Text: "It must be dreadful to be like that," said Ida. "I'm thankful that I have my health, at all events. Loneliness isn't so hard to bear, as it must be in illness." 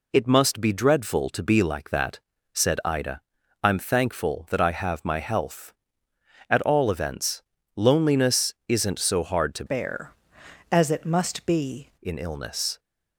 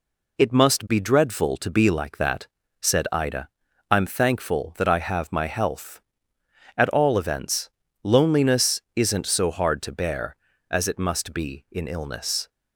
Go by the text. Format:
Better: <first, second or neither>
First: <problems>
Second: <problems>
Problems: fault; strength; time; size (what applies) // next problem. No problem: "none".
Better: second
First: pauses between "Loneliness" and "isn't"; slight; at 8.5 s; 0.16 s long // changes voice from "bear" to "be"; from 9.6 to 11.8 s; 2.2 s long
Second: pauses between "Loneliness" and "isn't"; slight; at 8.8 s; 0.16 s long